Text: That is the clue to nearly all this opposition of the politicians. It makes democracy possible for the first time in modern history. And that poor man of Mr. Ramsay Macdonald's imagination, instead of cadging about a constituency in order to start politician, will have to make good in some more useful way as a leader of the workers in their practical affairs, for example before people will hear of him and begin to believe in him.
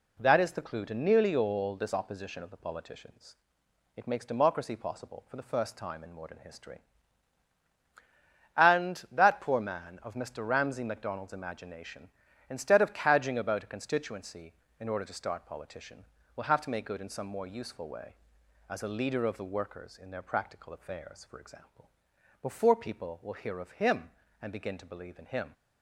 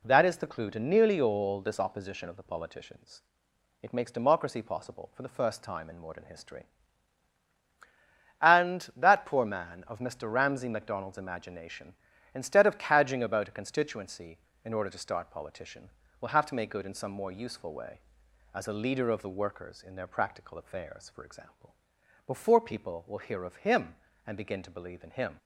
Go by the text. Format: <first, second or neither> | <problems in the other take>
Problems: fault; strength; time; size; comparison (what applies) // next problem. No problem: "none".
neither | pauses between "example" and "before"; noticeable; the same in both